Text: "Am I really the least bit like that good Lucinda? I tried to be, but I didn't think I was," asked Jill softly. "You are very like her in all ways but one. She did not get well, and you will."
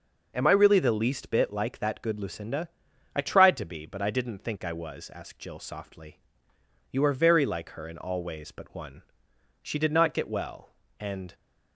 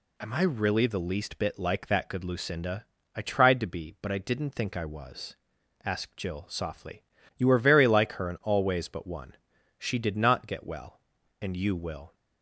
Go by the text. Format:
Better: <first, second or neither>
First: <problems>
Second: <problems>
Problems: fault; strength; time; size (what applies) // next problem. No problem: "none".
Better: second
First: stops before "you will"; at 11.3 s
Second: none